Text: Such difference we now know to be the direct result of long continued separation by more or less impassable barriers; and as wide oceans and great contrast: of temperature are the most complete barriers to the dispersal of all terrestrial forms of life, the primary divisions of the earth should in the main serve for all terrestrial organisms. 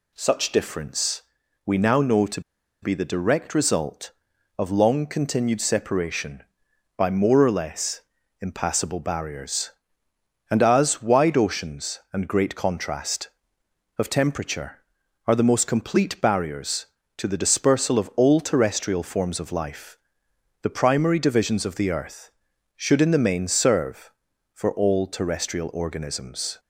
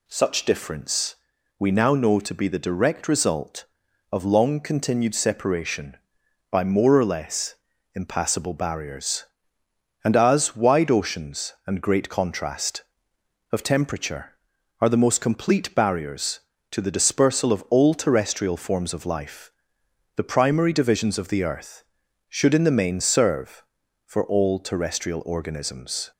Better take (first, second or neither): second